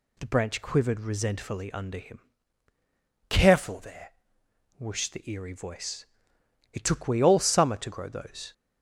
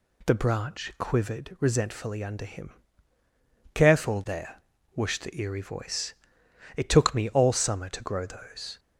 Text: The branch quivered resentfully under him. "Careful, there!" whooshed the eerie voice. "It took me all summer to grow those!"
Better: second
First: says "we" for "me"; at 7.0 s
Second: none

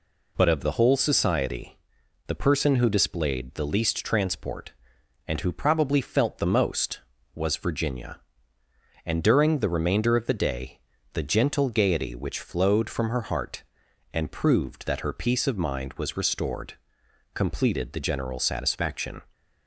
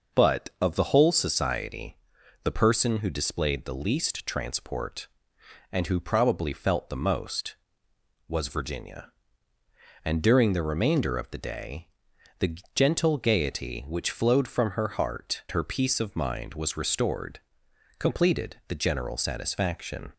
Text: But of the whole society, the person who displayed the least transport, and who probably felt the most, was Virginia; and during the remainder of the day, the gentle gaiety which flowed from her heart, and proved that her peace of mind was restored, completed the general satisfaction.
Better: first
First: none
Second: pauses between "the" and "gentle"; slight; at 12.5 s; 0.16 s long // skips "and proved that"; at 15.4 s

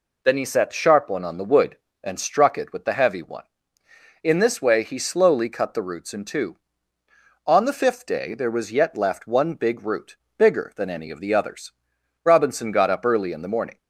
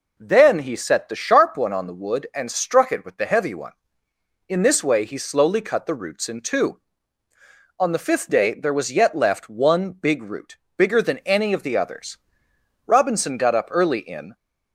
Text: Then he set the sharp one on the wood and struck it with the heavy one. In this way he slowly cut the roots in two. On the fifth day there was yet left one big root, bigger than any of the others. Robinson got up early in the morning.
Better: first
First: none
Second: stops before "the morning"; at 14.3 s

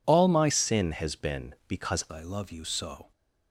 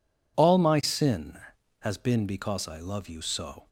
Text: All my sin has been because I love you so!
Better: second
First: changes voice from "sin" to "because"; from 0.4 to 2.0 s; 1.6 s long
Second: none

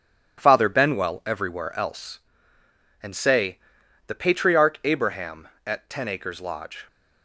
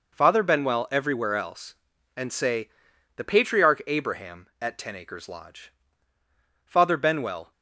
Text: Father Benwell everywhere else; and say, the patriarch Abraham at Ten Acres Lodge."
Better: first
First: none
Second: goes on to say "Father Benwell"; noticeable; from 6.6 s on; 0.86 s long

